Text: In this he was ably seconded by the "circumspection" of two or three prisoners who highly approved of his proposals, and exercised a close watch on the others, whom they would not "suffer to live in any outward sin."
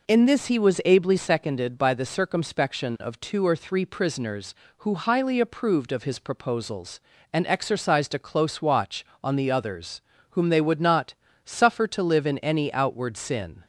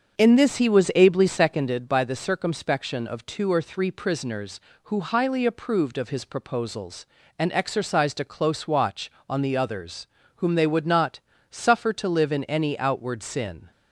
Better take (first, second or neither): first